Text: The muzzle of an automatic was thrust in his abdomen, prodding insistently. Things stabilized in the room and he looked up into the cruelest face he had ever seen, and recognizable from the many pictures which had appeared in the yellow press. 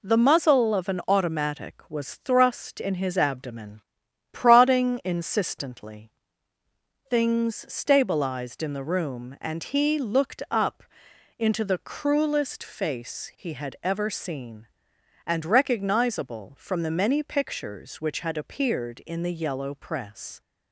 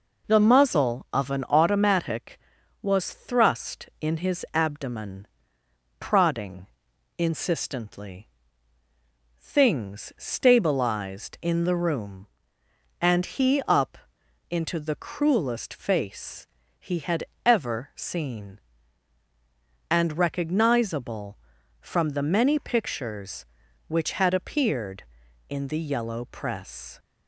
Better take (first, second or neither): first